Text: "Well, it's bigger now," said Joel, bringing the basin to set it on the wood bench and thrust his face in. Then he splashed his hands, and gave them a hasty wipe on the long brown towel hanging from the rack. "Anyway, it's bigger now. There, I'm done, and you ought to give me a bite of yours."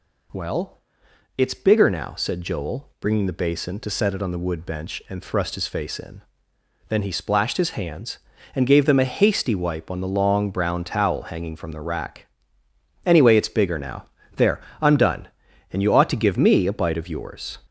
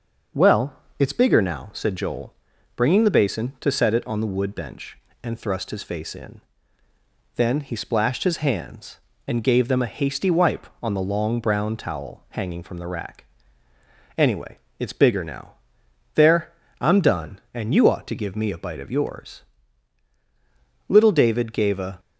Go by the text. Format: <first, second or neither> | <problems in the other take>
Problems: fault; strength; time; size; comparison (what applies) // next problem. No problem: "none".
first | starts louder than the rest; noticeable; until 1.5 s; 6 dB // goes on to say "Little David gave a"; noticeable; from 20.8 s on; 1.1 s long